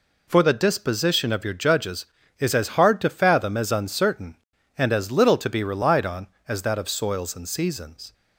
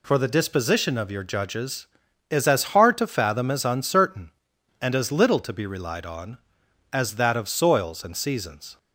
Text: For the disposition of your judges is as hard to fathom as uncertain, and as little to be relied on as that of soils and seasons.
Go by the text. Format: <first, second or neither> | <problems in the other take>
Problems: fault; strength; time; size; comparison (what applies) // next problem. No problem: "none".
neither | none